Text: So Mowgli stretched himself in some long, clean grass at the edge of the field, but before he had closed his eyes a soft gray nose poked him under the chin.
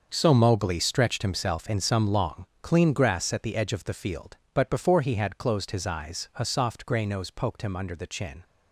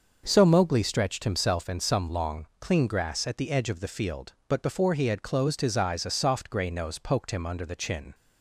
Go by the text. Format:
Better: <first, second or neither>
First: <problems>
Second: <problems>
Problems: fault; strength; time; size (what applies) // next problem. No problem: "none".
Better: second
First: gets quieter; strong; throughout; 12.5 dB // starts louder than the rest; until 1.1 s; 6 dB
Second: starts louder than the rest; until 1.2 s; 6 dB